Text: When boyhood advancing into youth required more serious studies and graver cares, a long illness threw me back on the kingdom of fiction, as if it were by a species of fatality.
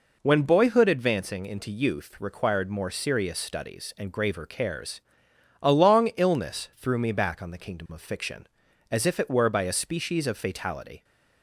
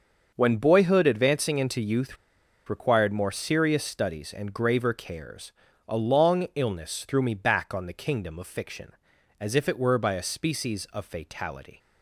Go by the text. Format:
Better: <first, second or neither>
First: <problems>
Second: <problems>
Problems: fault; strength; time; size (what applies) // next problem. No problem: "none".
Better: first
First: none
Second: starts louder than the rest; until 1.3 s; 6.5 dB // pauses between "youth" and "required"; noticeable; at 2.1 s; 0.52 s long